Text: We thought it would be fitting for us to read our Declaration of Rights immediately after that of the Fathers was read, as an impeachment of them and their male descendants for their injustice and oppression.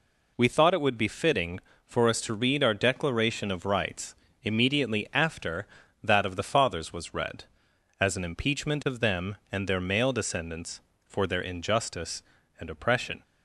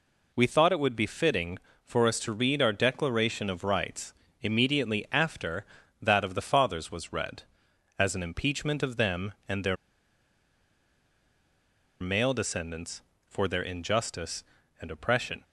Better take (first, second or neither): first